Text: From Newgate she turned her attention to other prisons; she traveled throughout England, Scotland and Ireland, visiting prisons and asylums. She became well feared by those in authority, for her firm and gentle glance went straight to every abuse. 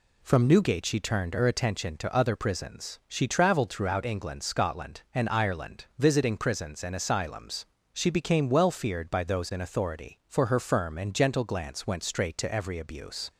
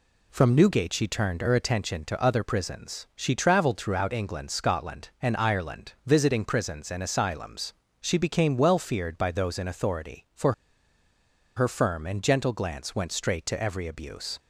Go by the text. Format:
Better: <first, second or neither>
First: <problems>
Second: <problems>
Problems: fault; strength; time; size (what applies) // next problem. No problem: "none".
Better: first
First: none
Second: pauses between "for" and "her"; at 10.5 s; 1.0 s long